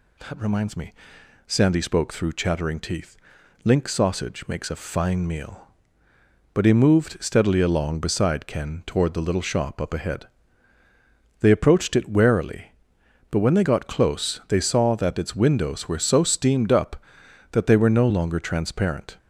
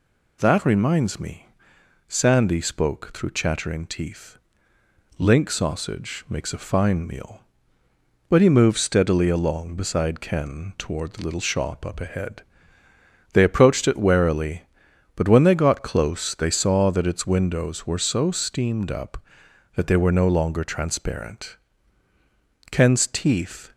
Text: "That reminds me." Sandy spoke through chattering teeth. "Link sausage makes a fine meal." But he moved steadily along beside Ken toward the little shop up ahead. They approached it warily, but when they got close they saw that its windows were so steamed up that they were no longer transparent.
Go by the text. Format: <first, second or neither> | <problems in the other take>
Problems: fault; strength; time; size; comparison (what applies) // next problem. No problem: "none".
first | goes on to say "Ken's teeth"; noticeable; from 22.7 s on; 1.0 s long